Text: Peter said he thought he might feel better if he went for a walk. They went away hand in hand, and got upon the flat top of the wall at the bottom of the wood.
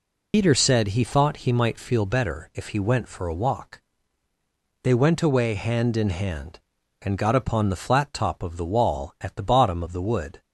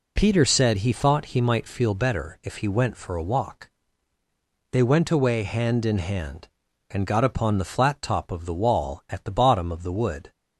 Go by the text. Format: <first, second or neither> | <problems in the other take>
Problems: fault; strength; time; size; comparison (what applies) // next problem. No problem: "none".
second | loses the start of "Peter"; at 0.3 s; 85 ms